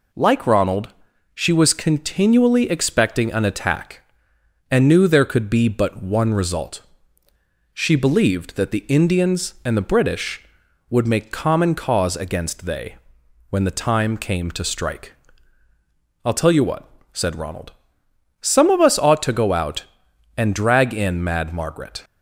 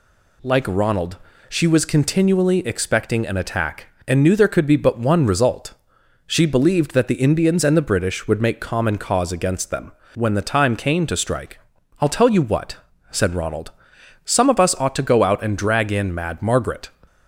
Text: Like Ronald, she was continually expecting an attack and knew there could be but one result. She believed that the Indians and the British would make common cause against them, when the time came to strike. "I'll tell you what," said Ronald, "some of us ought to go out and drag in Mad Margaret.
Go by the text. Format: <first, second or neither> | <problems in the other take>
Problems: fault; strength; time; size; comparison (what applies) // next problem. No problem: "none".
second | says "they" for "them"; at 12.6 s